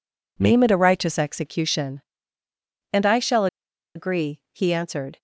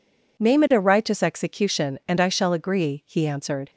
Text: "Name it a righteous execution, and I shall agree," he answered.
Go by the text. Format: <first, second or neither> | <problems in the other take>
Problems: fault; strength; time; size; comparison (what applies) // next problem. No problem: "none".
second | pauses between "shall" and "agree"; noticeable; at 3.4 s; 0.48 s long